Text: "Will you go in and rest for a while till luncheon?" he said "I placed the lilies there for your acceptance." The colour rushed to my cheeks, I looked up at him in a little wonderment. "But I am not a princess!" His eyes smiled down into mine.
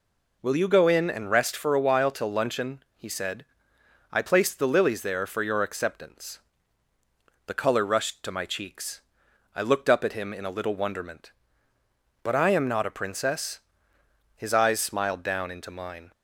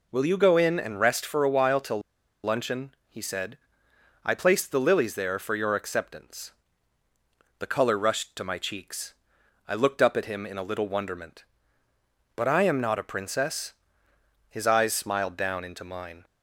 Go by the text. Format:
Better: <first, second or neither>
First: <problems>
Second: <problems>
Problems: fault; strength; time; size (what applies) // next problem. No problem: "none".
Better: first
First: pauses between "said" and "I"; noticeable; at 3.4 s; 0.66 s long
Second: pauses between "till" and "luncheon"; at 2.0 s; 0.43 s long // pauses between "said" and "I"; noticeable; at 3.5 s; 0.66 s long